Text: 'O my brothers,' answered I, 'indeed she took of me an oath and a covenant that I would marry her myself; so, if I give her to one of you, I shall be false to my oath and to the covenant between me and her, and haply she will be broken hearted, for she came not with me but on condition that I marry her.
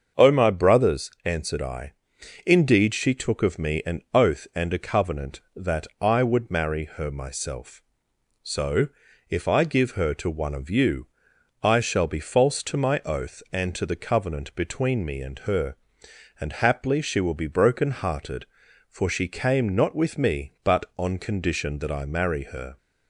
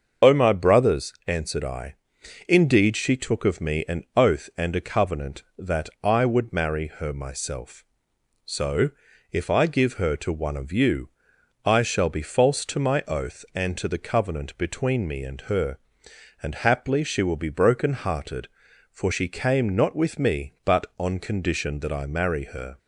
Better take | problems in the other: first | loses the start of "O"; at 0.2 s; 45 ms // starts louder than the rest; until 1.3 s; 6.5 dB; also in the first

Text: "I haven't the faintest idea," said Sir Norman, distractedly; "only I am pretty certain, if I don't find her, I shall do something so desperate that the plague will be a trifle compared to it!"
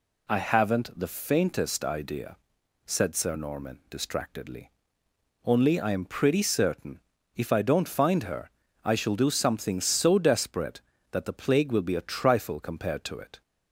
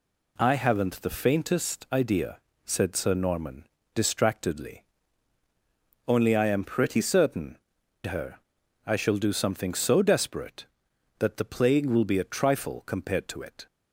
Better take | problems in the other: first | skips "if I don't find"; at 7.8 s

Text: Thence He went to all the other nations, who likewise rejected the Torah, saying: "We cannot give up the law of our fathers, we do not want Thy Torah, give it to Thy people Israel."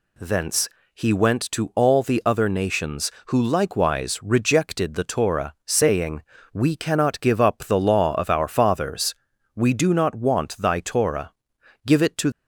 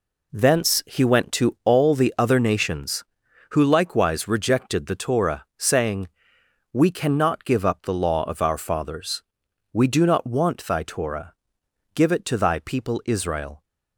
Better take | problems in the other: second | pauses between "Thence" and "He"; slight; at 0.6 s; 0.26 s long // stops before "Thy people Israel"; at 12.3 s

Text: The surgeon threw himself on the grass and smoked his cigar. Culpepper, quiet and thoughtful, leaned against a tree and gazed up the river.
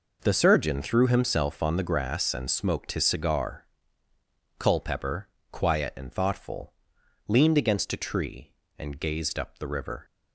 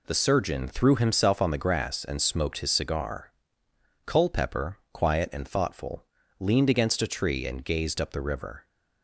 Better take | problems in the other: neither | none

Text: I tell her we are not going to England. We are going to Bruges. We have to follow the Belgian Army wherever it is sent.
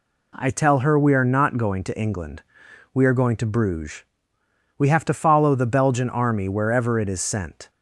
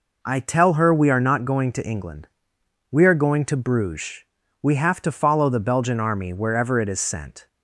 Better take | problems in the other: neither | none

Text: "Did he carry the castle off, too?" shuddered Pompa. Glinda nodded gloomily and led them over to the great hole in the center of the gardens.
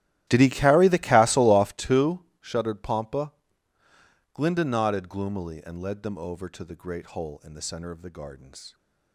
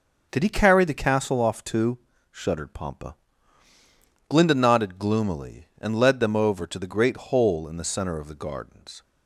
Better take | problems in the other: second | starts louder than the rest; strong; until 1.8 s; 14 dB

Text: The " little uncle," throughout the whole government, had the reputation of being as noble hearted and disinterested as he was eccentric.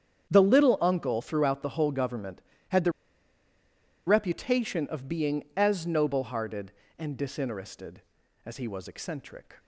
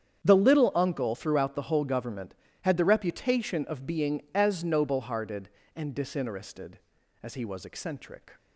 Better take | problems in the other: second | starts louder than the rest; strong; until 1.3 s; 8.5 dB; strong in the second // pauses between "the" and "reputation"; at 2.9 s; 1.1 s long

